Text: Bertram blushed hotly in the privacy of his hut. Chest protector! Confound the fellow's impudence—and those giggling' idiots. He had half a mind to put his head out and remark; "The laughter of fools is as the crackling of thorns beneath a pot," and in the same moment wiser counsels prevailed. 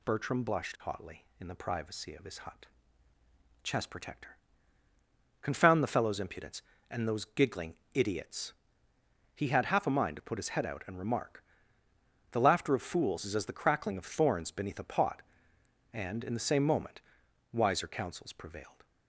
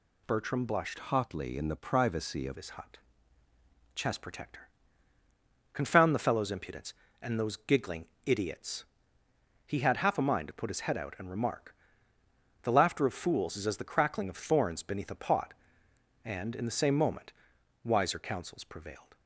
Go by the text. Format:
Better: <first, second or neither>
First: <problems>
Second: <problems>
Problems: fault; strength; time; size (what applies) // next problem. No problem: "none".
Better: first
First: pauses between "giggling" and "idiots"; slight; at 7.7 s; 0.20 s long // pauses between "moment" and "wiser"; noticeable; at 17.0 s; 0.50 s long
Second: changes voice from "hotly" to "of"; from 0.9 to 2.5 s; 1.6 s long // pauses between "giggling" and "idiots"; slight; at 8.0 s; 0.20 s long // pauses between "moment" and "wiser"; noticeable; at 17.3 s; 0.50 s long